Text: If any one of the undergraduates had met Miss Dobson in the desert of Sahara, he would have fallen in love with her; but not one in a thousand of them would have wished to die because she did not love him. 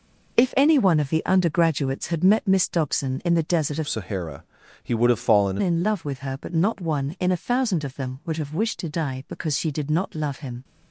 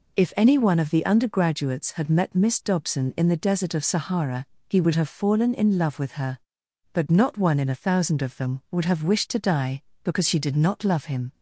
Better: second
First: changes voice from "Sahara" to "fallen"; from 3.8 to 5.5 s; 1.7 s long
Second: none

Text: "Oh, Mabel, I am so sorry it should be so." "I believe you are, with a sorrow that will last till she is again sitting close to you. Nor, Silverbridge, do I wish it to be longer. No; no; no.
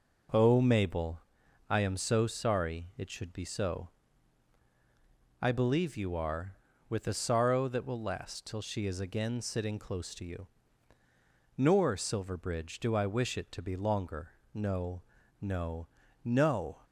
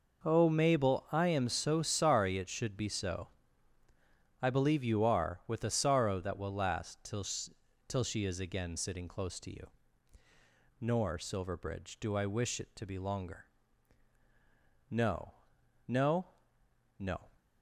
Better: first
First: none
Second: says "till" twice; at 7.8 s

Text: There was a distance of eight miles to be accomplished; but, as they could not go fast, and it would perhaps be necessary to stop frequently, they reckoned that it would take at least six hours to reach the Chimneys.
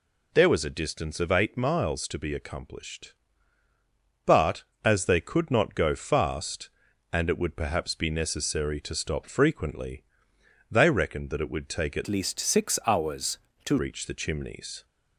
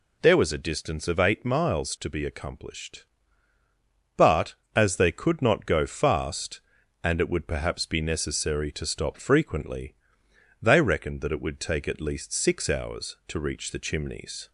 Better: second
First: changes voice from "least" to "to"; from 12.0 to 13.7 s; 1.7 s long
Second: none

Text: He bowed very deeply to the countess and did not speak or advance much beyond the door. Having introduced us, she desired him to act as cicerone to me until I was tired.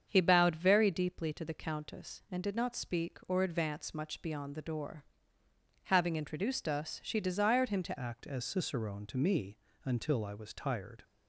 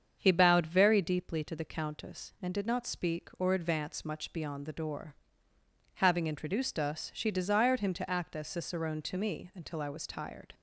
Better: second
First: starts louder than the rest; strong; until 1.0 s; 7.5 dB // changes voice at "act"; from 7.9 s on; 3.1 s long // pauses between "me" and "until"; slight; at 9.5 s; 0.26 s long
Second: starts louder than the rest; strong; until 1.1 s; 7.5 dB

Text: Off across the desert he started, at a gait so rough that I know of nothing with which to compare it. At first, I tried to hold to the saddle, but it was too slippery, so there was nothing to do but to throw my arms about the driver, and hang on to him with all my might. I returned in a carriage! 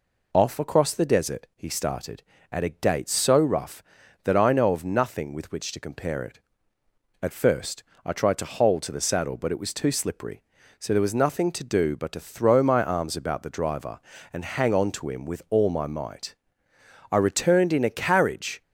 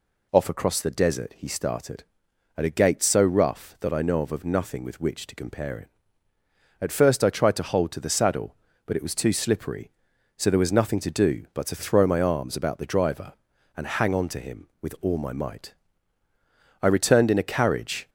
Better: first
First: none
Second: says "of" twice; at 4.3 s

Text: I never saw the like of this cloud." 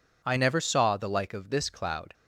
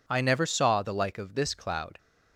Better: neither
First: none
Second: none

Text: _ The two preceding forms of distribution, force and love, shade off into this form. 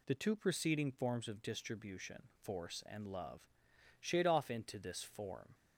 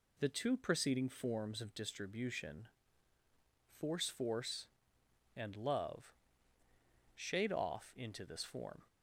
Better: first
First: none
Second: says "force" twice; at 4.0 s

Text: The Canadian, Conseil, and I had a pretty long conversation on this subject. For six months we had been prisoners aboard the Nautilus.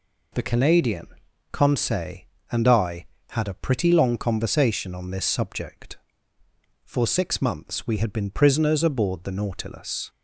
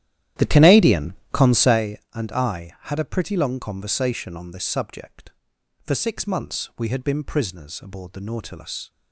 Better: first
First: none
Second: starts louder than the rest; strong; until 1.8 s; 12 dB

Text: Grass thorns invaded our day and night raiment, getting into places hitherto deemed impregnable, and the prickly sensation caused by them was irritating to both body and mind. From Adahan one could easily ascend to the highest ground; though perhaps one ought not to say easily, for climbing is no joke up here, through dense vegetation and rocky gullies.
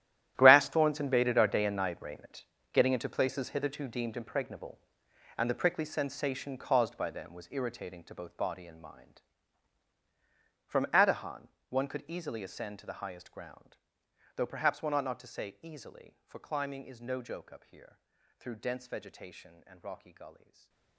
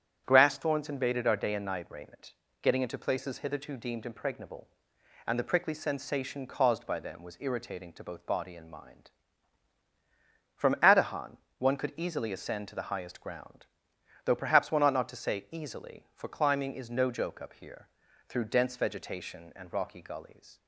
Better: second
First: gets quieter; strong; throughout; 16.5 dB // starts louder than the rest; strong; until 1.3 s; 12 dB // pauses between "Adahan" and "one"; slight; at 11.4 s; 0.22 s long // stays silent after the last word; slight; from 20.3 s on; 0.6 s long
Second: starts louder than the rest; strong; until 1.2 s; 8.5 dB // pauses between "Adahan" and "one"; slight; at 11.3 s; 0.22 s long

